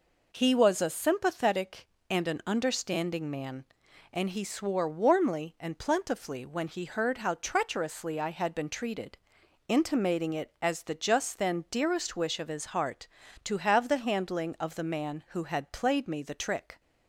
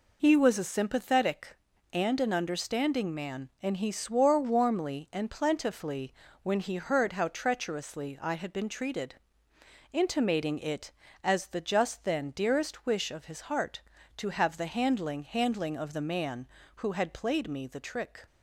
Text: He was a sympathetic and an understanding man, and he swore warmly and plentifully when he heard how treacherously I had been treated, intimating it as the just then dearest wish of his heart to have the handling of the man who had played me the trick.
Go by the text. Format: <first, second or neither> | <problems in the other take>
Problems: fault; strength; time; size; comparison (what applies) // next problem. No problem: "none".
first | pauses between "plentifully" and "when"; slight; at 6.1 s; 0.30 s long // says "handling" twice; at 15.2 s